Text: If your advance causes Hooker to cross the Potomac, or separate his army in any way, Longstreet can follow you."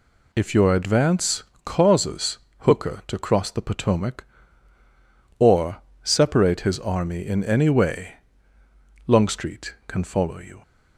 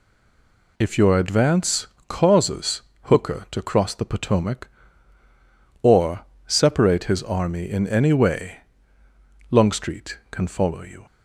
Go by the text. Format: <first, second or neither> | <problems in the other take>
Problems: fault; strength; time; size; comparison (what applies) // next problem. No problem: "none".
first | stays silent before the first word; slight; until 0.7 s; 0.7 s long // pauses between "advance" and "causes"; slight; at 1.8 s; 0.22 s long; slight in the first // pauses between "causes" and "Hooker"; slight; at 2.8 s; 0.22 s long; slight in the first // pauses between "or" and "separate"; slight; at 6.2 s; 0.22 s long; slight in the first